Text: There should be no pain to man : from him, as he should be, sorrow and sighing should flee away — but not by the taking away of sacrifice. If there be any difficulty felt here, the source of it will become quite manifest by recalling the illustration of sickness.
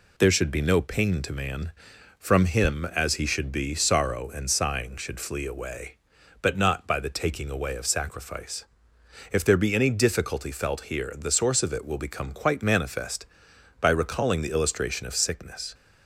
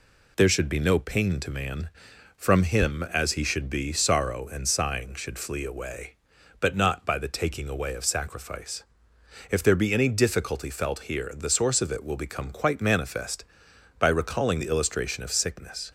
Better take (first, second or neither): neither